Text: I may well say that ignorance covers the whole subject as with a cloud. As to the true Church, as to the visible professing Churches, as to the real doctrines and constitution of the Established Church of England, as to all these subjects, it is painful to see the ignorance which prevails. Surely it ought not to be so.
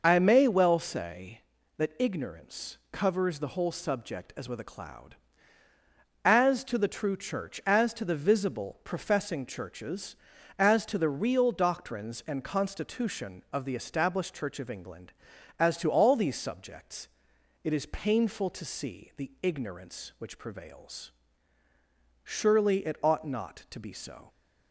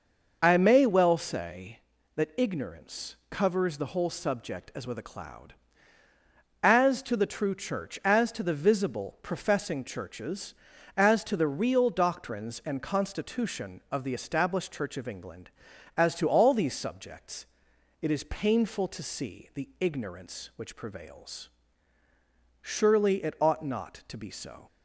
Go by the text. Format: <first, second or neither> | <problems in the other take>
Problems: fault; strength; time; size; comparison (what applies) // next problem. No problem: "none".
neither | pauses between "ignorance" and "covers"; slight; the same in both